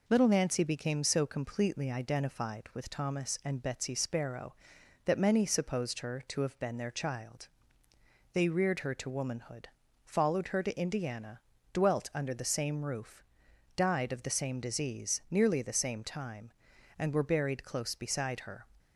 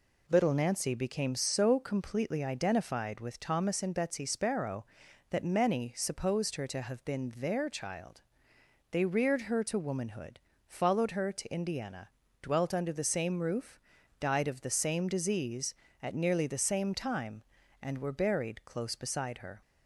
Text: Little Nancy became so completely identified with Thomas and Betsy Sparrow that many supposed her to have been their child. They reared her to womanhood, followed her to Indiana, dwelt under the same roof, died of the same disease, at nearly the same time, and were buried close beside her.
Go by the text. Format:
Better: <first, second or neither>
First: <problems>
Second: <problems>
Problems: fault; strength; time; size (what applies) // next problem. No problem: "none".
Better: second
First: skips "at"; at 15.2 s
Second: none